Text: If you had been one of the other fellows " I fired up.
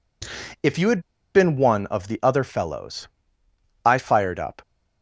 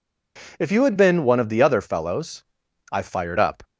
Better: second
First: pauses between "had" and "been"; slight; at 1.0 s; 0.34 s long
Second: none

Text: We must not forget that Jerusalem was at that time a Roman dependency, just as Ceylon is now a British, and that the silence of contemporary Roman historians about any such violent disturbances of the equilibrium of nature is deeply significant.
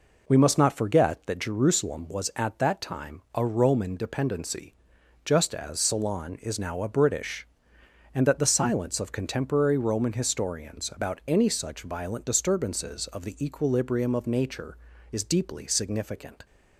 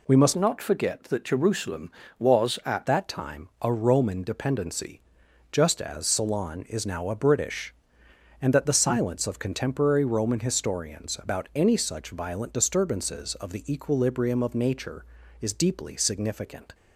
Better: first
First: none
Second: changes voice from "not" to "at"; from 0.3 to 2.8 s; 2.5 s long

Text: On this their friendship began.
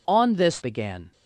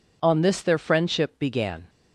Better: second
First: skips "their friendship"; at 0.6 s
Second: none

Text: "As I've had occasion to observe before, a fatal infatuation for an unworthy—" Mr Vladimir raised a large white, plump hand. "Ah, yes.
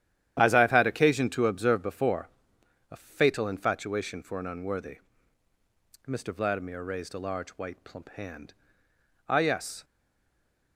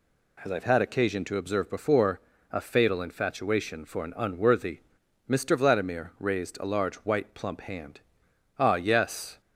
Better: second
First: starts louder than the rest; strong; until 1.3 s; 11 dB // stays silent after the last word; slight; from 9.8 s on; 0.9 s long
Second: none

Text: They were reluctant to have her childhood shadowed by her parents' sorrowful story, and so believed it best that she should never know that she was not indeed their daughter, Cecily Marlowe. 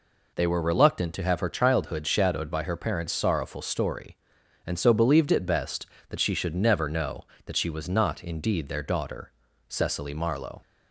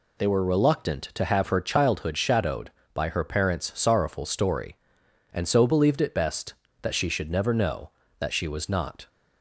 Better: first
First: none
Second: stops before "indeed their daughter Cecily Marlowe"; at 9.0 s

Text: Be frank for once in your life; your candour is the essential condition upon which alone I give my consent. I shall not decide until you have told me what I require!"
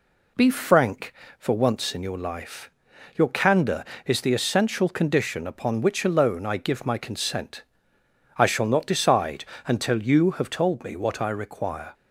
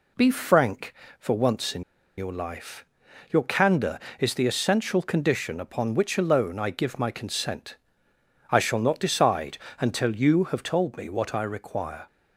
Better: first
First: pauses between "decide" and "until"; slight; at 9.4 s; 0.20 s long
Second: pauses between "in" and "your"; slight; at 1.8 s; 0.35 s long // pauses between "decide" and "until"; slight; at 9.5 s; 0.20 s long

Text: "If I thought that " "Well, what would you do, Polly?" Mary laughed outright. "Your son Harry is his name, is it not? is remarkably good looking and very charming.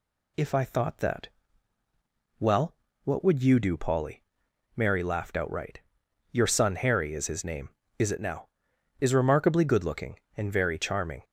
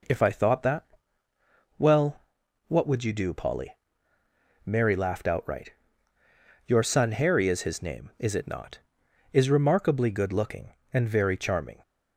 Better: second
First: says "now" for "not"; at 8.1 s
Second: none

